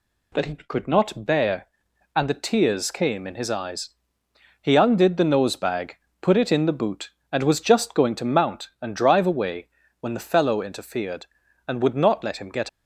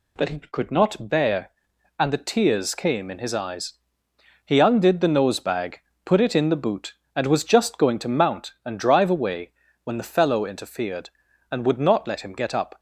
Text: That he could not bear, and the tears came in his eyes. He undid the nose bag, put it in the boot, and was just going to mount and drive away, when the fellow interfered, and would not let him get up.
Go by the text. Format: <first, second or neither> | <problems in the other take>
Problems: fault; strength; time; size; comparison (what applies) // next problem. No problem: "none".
second | stops before "up"; at 12.6 s